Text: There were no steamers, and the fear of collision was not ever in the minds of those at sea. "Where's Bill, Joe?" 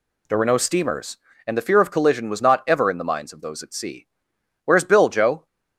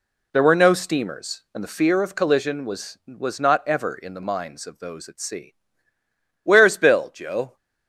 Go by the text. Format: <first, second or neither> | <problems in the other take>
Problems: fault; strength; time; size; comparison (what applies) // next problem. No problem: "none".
first | says "was" twice; at 3.0 s